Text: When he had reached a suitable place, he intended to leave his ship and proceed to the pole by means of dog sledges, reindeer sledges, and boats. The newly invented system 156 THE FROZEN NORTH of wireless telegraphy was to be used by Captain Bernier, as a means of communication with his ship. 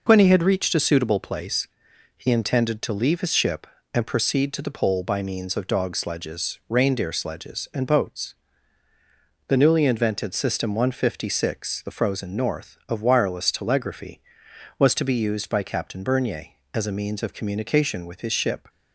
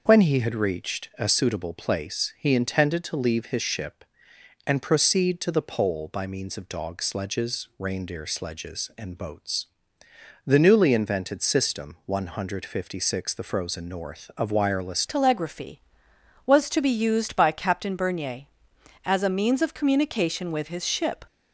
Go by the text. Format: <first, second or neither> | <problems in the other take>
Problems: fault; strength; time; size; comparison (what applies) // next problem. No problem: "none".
first | changes voice at "telegraphy"; from 15.0 s on; 6.2 s long